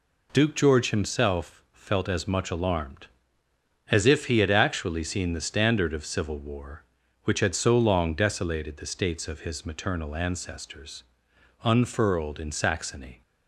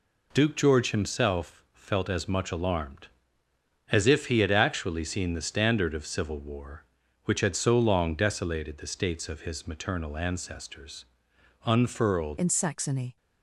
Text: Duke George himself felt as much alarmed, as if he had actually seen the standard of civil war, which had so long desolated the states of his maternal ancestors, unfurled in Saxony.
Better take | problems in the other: first | changes voice at "in"; from 12.3 s on; 0.8 s long

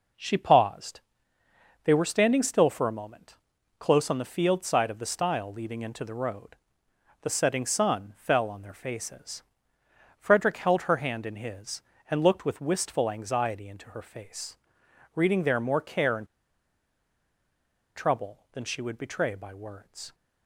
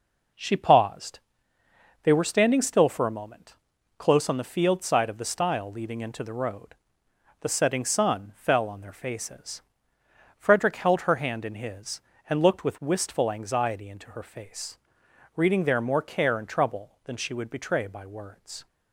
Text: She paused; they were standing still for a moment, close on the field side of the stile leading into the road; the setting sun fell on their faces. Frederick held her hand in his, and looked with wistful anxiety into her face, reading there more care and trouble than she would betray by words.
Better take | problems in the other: second | pauses between "and" and "trouble"; strong; at 16.2 s; 1.7 s long

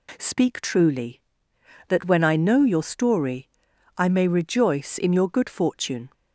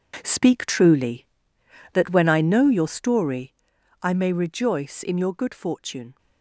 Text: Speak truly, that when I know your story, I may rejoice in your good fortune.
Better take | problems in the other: first | gets quieter; strong; throughout; 11.5 dB

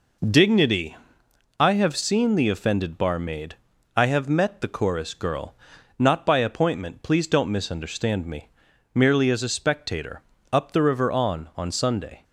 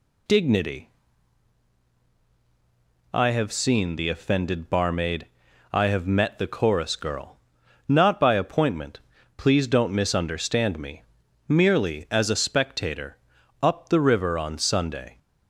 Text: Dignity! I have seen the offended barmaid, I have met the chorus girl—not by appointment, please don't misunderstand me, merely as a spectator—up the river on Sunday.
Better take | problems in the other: second | says "on" twice; at 11.5 s

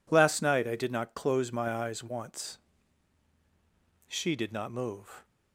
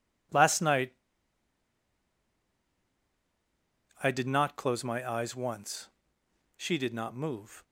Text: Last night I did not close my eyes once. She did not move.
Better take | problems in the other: first | pauses between "night" and "I"; strong; at 0.9 s; 3.0 s long

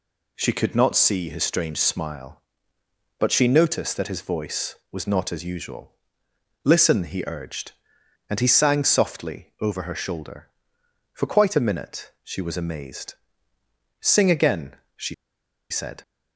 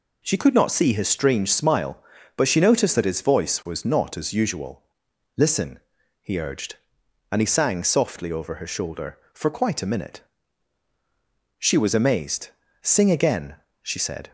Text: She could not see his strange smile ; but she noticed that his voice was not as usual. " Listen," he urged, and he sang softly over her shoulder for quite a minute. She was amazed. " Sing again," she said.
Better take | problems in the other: second | pauses between "she" and "said"; noticeable; at 15.1 s; 0.56 s long

